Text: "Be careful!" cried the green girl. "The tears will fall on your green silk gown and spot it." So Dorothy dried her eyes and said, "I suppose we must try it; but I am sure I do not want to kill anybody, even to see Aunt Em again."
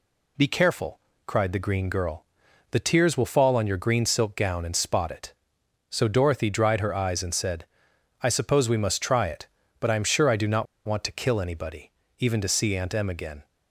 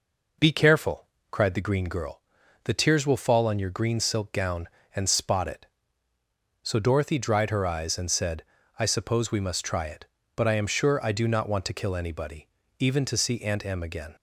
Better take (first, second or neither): second